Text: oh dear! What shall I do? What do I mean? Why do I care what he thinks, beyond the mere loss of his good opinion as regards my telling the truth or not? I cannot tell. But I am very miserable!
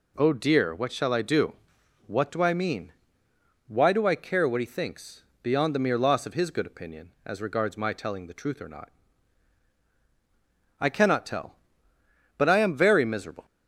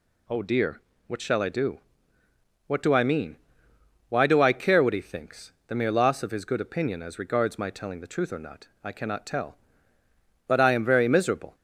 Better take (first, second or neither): first